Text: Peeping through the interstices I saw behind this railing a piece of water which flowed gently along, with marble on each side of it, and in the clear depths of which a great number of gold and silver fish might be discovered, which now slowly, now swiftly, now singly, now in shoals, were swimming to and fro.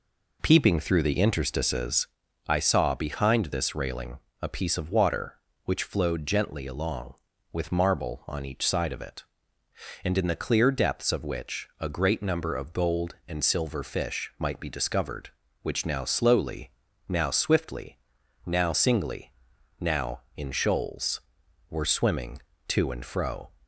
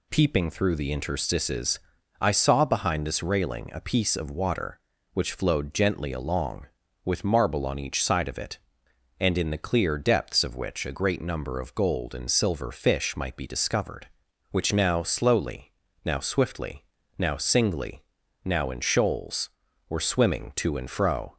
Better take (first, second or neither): second